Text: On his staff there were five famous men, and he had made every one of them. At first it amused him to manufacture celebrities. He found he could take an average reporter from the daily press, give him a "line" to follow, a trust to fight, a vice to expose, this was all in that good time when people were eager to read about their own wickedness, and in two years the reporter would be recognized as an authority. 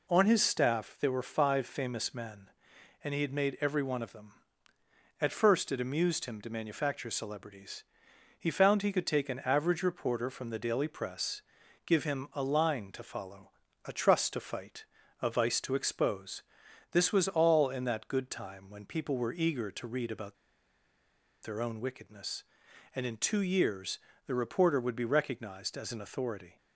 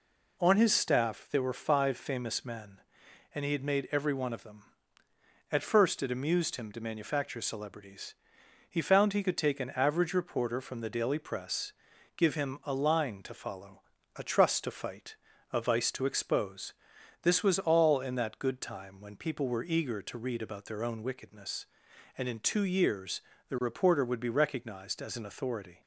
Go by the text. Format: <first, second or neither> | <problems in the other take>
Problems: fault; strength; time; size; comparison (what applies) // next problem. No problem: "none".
second | pauses between "about" and "their"; at 20.3 s; 1.0 s long // pauses between "years" and "the"; slight; at 23.9 s; 0.28 s long; slight in the second